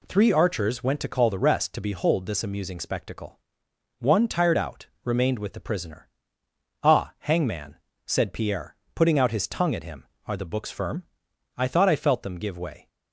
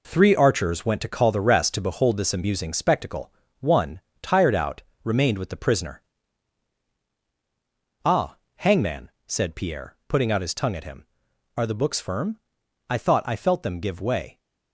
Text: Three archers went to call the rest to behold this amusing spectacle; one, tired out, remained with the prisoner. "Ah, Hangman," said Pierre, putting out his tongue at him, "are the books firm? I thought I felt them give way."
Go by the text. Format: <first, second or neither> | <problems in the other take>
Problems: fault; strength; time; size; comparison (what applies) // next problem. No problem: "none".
first | gets quieter; strong; throughout; 7.5 dB